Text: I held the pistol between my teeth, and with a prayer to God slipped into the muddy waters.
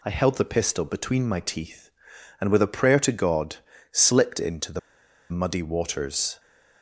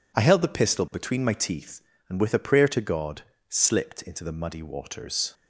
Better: second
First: pauses between "God" and "slipped"; slight; at 3.5 s; 0.34 s long // pauses between "the" and "muddy"; noticeable; at 4.7 s; 0.52 s long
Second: pauses between "God" and "slipped"; slight; at 3.2 s; 0.28 s long

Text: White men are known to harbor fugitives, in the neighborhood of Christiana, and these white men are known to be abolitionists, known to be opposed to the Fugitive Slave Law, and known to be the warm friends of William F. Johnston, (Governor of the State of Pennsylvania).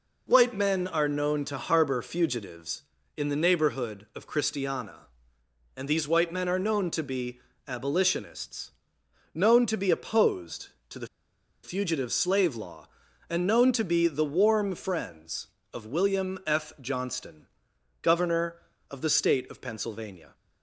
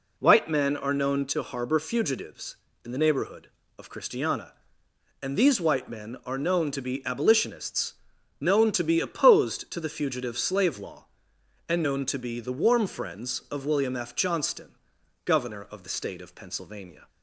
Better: second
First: pauses between "be" and "abolitionists"; slight; at 7.3 s; 0.26 s long // pauses between "the" and "Fugitive"; noticeable; at 11.0 s; 0.57 s long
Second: none

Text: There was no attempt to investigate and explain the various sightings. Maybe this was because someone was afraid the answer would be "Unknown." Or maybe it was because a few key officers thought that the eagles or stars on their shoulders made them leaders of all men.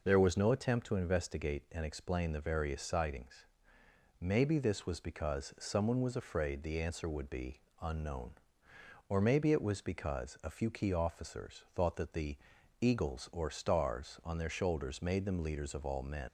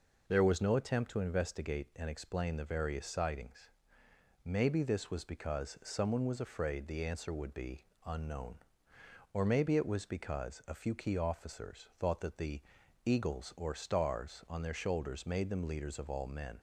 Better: second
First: pauses between "be" and "Unknown"; slight; at 7.5 s; 0.20 s long // pauses between "the" and "eagles"; at 12.3 s; 0.44 s long // leaves "men" unfinished; at 16.2 s; 60 ms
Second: pauses between "be" and "Unknown"; slight; at 7.8 s; 0.20 s long // pauses between "the" and "eagles"; at 12.6 s; 0.44 s long

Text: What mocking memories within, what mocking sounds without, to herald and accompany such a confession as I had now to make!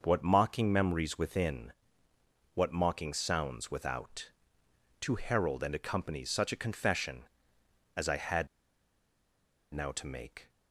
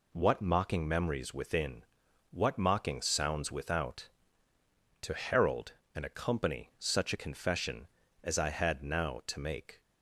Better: second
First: pauses between "had" and "now"; strong; at 8.4 s; 1.2 s long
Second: none

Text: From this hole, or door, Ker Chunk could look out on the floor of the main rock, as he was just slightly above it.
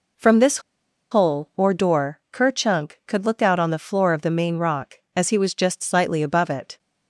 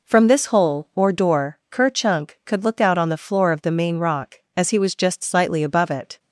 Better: second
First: pauses between "this" and "hole"; noticeable; at 0.5 s; 0.52 s long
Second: none

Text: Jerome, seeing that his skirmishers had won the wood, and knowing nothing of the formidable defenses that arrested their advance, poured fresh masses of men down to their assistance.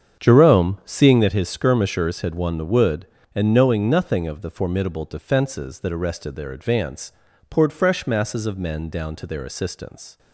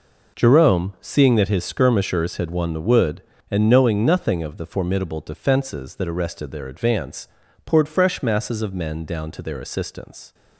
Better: second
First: starts louder than the rest; strong; until 1.3 s; 7.5 dB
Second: none

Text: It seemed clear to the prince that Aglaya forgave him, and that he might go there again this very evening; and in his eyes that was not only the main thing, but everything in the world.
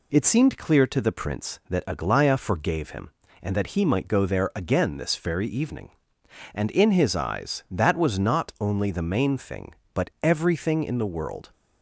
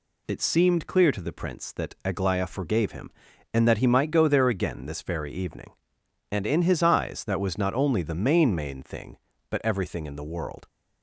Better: first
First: none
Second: says "main" twice; at 8.5 s

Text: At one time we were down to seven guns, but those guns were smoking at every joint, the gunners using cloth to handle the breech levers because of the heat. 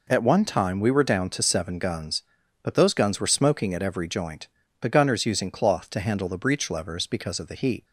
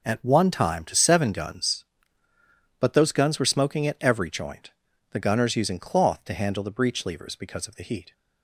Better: first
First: none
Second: skips "we were down"; at 0.8 s

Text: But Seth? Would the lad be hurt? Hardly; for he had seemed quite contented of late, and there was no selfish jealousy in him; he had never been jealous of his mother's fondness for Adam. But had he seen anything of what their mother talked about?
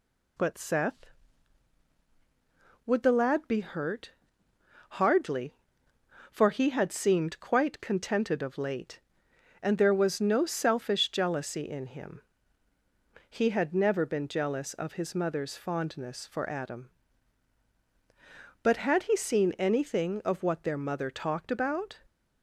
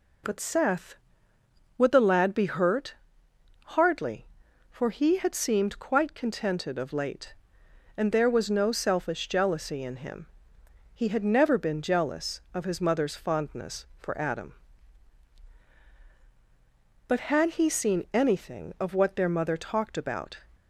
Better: neither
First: none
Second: none

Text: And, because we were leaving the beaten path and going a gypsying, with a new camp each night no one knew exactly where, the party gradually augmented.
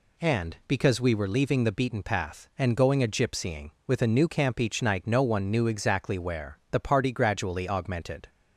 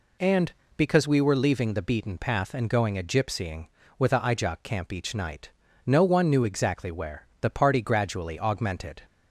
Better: first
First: none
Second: says "ijok" for "new"; at 4.1 s // pauses between "night" and "no"; slight; at 5.5 s; 0.36 s long

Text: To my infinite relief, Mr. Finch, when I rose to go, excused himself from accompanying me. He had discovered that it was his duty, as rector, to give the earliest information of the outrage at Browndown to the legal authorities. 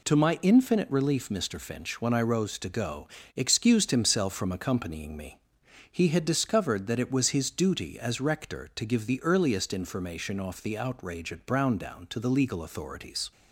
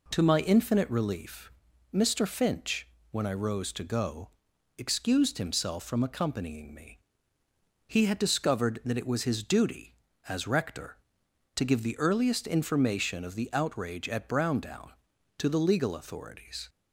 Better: second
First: says "off" for "of"; at 10.3 s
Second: none

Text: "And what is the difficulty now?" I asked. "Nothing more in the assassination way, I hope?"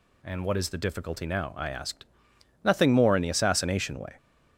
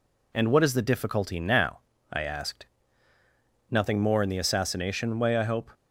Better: second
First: stops before "I hope"; at 4.1 s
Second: none

